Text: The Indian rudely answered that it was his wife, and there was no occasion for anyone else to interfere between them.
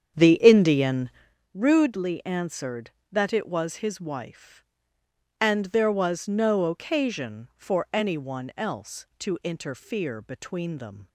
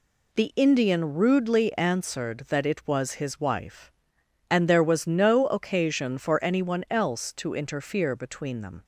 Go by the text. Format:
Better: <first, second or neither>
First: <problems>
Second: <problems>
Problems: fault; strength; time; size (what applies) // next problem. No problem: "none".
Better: second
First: starts louder than the rest; strong; until 1.4 s; 8 dB // pauses between "Indian" and "rudely"; at 1.0 s; 0.44 s long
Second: none